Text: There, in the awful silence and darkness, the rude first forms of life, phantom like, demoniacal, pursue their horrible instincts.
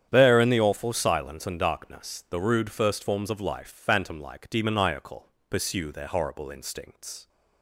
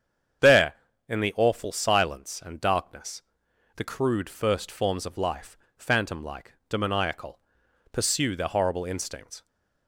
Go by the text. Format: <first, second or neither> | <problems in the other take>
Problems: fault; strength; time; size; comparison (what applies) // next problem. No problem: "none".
first | starts louder than the rest; strong; until 1.8 s; 8 dB; strong in the first // says "crude" for "rude"; at 3.8 s